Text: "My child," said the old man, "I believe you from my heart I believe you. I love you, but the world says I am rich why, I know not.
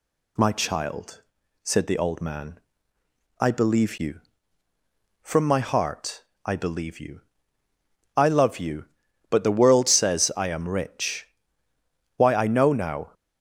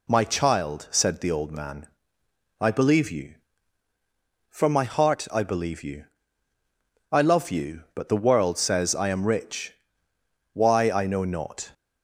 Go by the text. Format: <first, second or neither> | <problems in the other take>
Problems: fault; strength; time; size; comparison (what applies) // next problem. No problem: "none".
second | pauses between "heart" and "I"; slight; at 6.2 s; 0.20 s long // pauses between "rich" and "why"; noticeable; at 11.2 s; 0.90 s long; noticeable in the second // says "now" for "not"; at 12.7 s